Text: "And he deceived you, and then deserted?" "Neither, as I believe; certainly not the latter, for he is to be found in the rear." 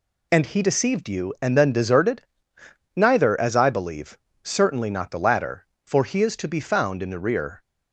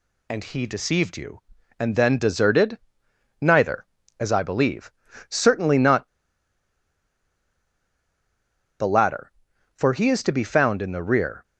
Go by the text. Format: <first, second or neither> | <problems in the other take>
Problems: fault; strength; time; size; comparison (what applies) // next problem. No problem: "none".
first | pauses between "not" and "the"; strong; at 6.0 s; 2.7 s long